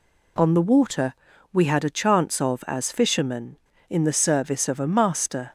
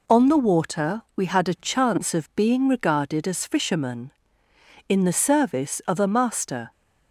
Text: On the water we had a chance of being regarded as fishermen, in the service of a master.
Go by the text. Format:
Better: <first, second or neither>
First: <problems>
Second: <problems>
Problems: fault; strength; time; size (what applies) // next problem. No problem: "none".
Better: second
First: pauses between "water" and "we"; slight; at 1.1 s; 0.36 s long // skips "being regarded"; at 2.6 s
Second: none